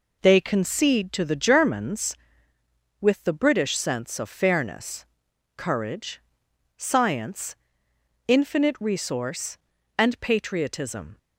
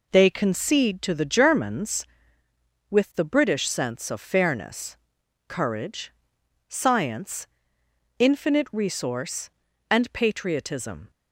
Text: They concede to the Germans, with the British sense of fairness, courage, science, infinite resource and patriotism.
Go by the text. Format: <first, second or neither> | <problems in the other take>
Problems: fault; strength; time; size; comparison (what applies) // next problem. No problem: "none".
neither | none